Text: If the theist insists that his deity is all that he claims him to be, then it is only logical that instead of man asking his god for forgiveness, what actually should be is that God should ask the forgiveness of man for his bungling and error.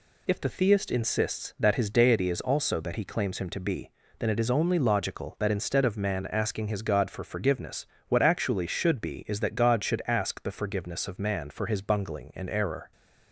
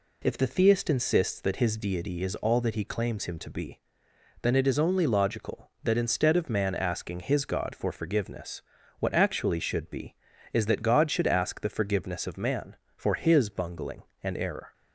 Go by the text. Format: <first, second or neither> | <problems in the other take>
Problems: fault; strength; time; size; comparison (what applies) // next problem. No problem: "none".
second | says "also" for "all"; at 2.4 s